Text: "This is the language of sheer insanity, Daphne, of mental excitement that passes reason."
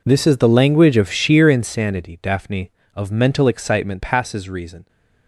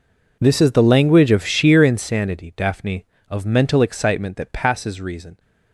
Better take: second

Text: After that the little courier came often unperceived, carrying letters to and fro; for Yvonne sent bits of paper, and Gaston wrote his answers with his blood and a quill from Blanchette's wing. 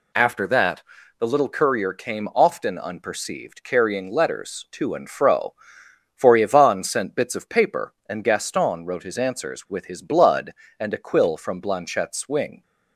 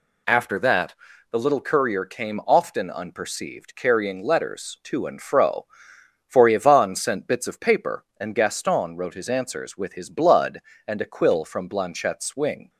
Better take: neither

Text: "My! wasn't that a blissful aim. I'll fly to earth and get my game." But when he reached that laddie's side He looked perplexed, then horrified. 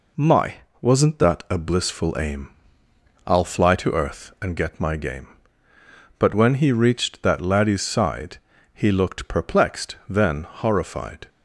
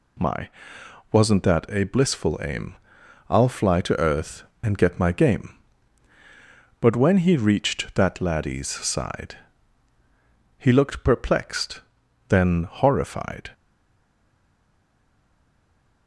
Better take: first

